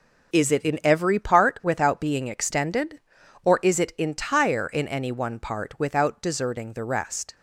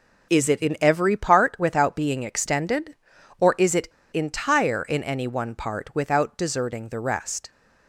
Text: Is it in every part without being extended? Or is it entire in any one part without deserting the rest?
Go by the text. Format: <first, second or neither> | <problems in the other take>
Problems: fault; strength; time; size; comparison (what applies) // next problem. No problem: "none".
first | starts louder than the rest; noticeable; until 1.3 s; 6 dB // pauses between "it" and "entire"; slight; at 3.8 s; 0.24 s long